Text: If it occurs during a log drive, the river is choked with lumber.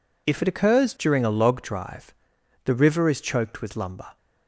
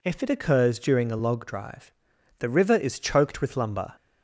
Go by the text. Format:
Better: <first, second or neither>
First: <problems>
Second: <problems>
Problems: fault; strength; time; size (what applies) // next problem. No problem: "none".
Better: neither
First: none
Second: none